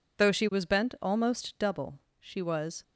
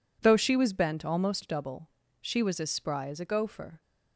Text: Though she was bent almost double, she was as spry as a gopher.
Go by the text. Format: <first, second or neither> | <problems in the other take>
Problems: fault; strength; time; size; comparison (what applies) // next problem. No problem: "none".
second | stops before "as spry as a gopher"; at 2.8 s